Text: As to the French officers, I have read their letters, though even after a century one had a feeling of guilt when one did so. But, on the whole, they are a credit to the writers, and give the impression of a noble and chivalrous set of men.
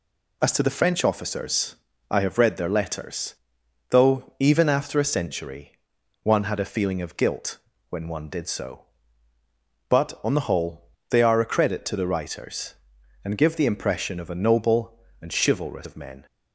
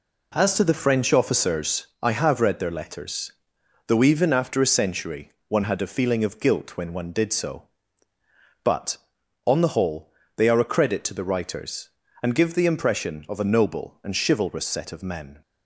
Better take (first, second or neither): second